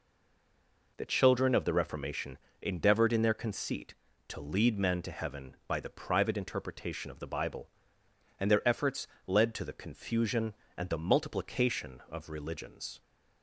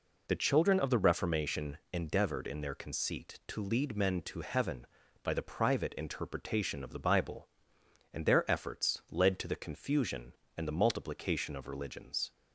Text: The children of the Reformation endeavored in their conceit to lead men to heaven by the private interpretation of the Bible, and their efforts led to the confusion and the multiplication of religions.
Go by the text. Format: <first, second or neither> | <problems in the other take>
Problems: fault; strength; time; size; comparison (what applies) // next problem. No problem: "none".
second | stays silent before the first word; until 0.9 s; 0.9 s long // pauses between "Reformation" and "endeavored"; slight; at 2.3 s; 0.24 s long // pauses between "efforts" and "led"; slight; at 9.0 s; 0.18 s long